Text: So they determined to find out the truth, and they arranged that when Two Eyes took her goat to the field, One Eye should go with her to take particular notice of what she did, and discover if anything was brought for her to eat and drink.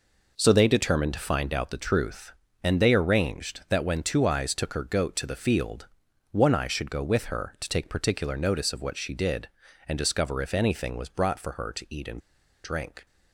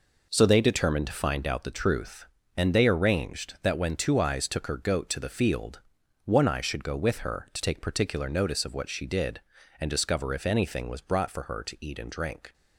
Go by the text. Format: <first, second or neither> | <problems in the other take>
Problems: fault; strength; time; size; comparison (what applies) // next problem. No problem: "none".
second | pauses between "and" and "drink"; at 12.2 s; 0.44 s long